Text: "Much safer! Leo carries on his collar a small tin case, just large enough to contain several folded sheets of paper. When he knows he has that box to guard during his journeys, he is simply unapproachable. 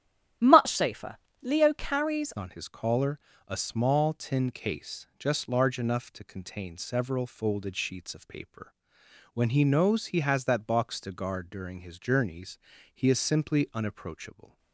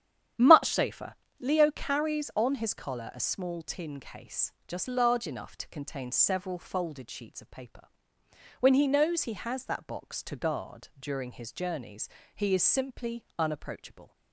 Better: second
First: starts louder than the rest; strong; until 1.6 s; 11.5 dB // changes voice at "on"; from 2.3 s on; 12.2 s long // pauses between "collar" and "a"; slight; at 3.1 s; 0.28 s long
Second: starts louder than the rest; strong; until 1.6 s; 10 dB

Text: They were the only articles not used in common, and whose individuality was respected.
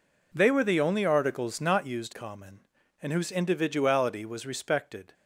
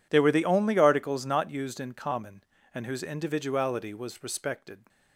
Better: second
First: skips "in"; at 2.1 s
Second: none

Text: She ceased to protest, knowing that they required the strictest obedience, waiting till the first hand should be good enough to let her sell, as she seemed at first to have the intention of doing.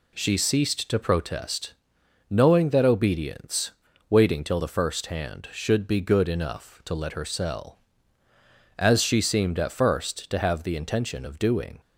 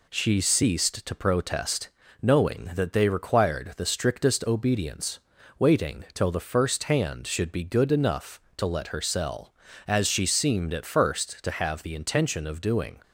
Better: second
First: skips "they required the strictest"; at 2.8 s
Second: none

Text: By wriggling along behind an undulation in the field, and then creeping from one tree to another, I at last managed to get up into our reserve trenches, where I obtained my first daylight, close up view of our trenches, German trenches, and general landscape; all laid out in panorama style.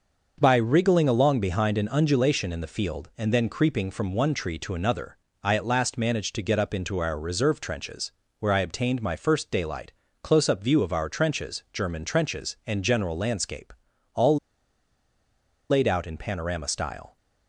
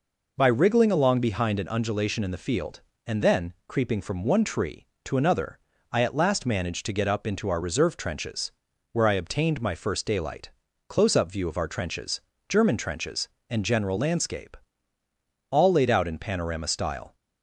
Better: second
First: starts louder than the rest; until 1.4 s; 6 dB // pauses between "all" and "laid"; strong; at 14.3 s; 1.3 s long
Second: none

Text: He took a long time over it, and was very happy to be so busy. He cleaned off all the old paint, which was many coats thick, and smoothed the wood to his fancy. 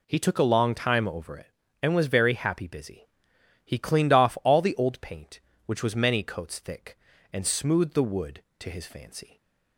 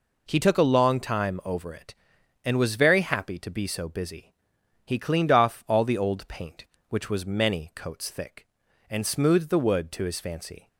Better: second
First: skips "to be so"; at 2.6 s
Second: none

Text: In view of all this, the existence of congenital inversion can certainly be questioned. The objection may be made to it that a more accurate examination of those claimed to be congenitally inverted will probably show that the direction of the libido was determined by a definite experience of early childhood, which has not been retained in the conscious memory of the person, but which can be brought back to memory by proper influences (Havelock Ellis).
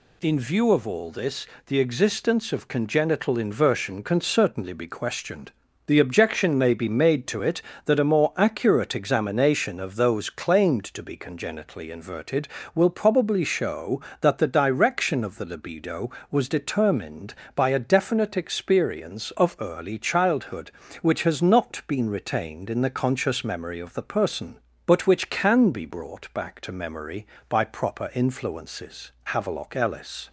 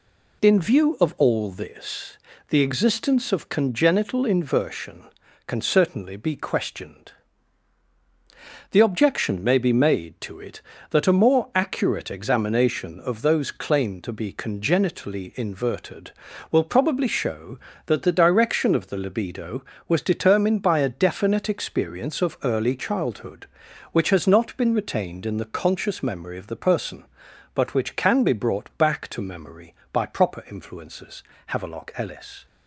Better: neither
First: none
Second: none

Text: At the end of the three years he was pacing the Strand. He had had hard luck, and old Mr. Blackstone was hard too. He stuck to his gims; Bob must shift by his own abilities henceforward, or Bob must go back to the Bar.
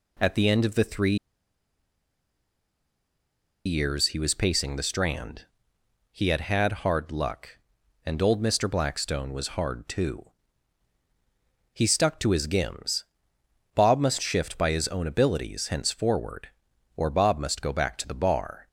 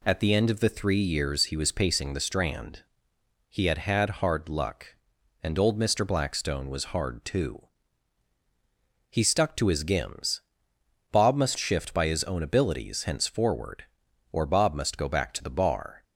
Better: second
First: pauses between "three" and "years"; strong; at 1.1 s; 2.4 s long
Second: none

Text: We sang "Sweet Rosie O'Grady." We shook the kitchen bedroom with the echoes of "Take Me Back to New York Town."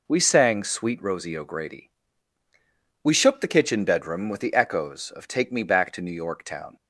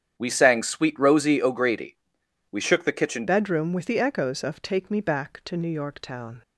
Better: first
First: none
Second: starts louder than the rest; strong; until 1.1 s; 9 dB // changes voice at "bedroom"; from 3.2 s on; 3.2 s long

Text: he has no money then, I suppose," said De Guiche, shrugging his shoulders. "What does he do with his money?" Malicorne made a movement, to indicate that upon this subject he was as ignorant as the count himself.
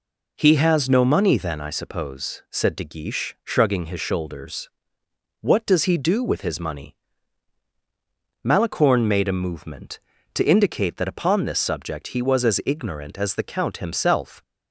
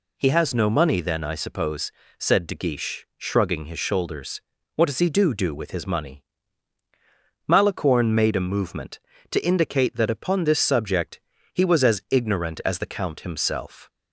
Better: first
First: none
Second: says "do" twice; at 5.3 s // pauses between "subject" and "he"; slight; at 11.1 s; 0.34 s long

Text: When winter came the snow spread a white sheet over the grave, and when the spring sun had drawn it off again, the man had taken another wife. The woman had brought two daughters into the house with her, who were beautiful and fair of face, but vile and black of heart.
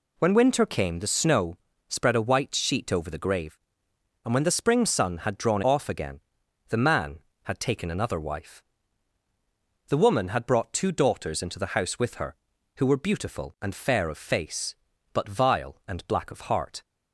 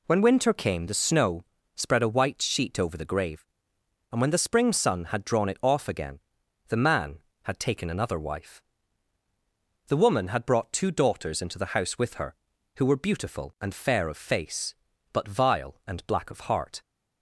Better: second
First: pauses between "snow" and "spread"; slight; at 1.5 s; 0.30 s long // skips "it"; at 5.6 s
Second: pauses between "snow" and "spread"; slight; at 1.4 s; 0.30 s long

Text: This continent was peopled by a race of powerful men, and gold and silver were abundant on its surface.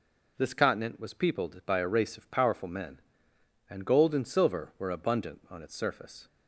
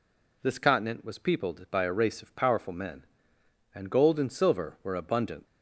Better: first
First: none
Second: stops before "on its surface"; at 5.4 s

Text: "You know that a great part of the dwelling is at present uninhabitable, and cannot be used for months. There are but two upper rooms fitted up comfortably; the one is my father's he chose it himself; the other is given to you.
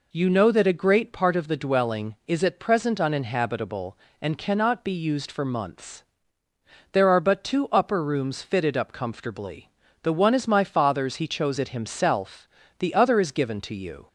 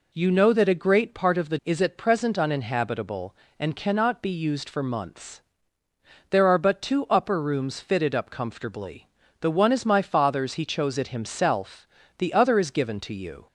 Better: first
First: none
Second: skips "dwelling"; at 1.6 s

